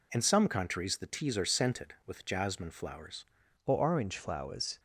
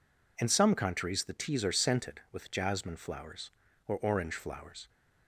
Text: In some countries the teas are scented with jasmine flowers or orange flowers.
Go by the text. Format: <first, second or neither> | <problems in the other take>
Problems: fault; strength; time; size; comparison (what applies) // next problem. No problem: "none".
second | changes voice at "or"; from 3.6 s on; 1.1 s long